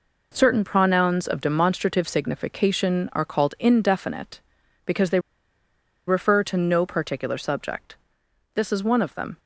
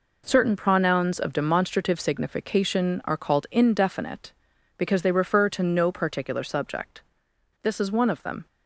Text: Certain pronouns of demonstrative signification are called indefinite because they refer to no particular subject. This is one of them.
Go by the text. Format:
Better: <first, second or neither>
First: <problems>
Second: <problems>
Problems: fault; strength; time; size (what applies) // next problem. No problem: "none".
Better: second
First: pauses between "they" and "refer"; noticeable; at 5.1 s; 0.88 s long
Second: none